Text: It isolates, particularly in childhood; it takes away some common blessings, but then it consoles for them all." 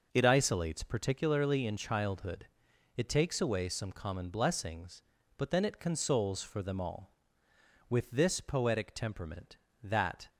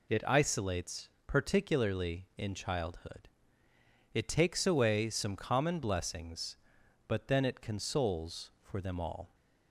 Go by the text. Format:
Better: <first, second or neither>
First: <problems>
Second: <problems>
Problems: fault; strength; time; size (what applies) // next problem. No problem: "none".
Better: second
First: goes on to say "With this poetic temperament that"; strong; from 7.8 s on; 2.4 s long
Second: none